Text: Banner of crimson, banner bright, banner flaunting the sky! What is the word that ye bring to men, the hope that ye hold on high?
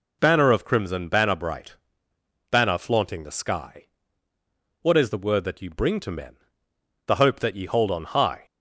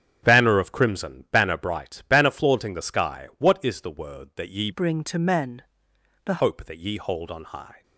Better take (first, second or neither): first